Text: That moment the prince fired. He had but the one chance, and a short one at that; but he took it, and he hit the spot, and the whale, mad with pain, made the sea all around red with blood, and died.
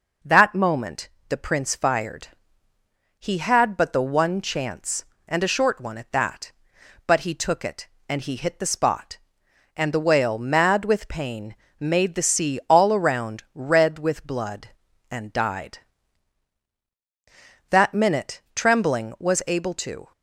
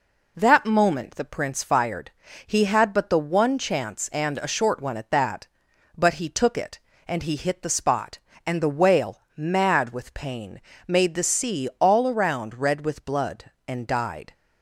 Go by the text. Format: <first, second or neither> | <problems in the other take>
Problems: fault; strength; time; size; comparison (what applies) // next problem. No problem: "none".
second | pauses between "moment" and "the"; slight; at 1.0 s; 0.22 s long // goes on to say "That minute Trembling was able to"; strong; from 17.6 s on; 2.4 s long